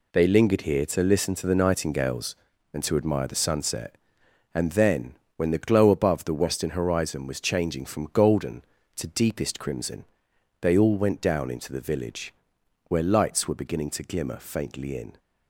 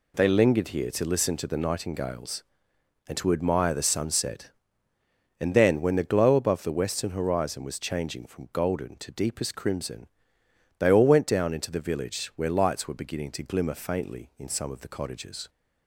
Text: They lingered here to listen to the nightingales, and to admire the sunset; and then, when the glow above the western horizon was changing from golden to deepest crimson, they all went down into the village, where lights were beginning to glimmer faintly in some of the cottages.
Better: second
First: stops before "some of the cottages"; at 15.1 s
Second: none

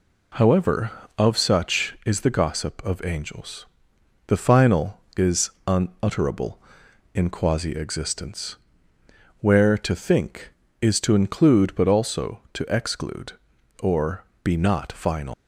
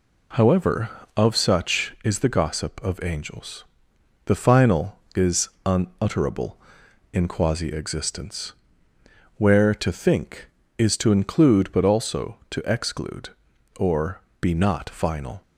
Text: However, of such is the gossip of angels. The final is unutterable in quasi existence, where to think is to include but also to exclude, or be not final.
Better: second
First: pauses between "is" and "unutterable"; slight; at 5.5 s; 0.16 s long // pauses between "or" and "be"; slight; at 14.2 s; 0.19 s long // leaves "final" unfinished; at 15.3 s; 105 ms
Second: pauses between "is" and "unutterable"; slight; at 5.4 s; 0.16 s long // pauses between "or" and "be"; slight; at 14.1 s; 0.20 s long

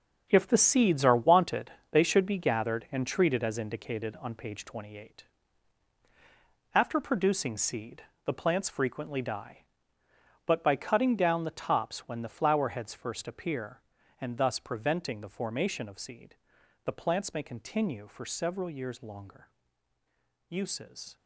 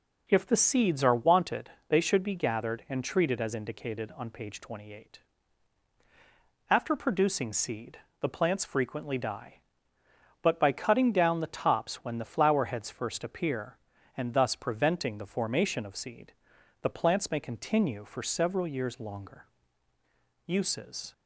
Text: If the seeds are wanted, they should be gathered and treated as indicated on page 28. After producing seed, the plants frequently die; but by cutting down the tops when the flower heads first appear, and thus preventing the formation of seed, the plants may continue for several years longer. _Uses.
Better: second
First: gets quieter; strong; throughout; 10.5 dB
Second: none

